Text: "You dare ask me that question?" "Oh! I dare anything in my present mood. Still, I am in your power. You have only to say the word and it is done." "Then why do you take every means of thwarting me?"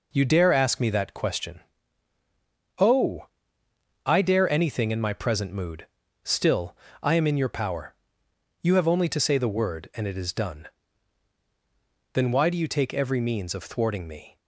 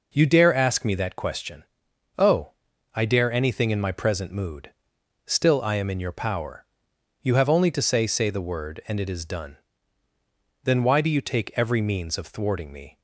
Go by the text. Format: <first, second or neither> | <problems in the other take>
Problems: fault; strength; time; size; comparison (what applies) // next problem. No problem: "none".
first | says "say" twice; at 8.0 s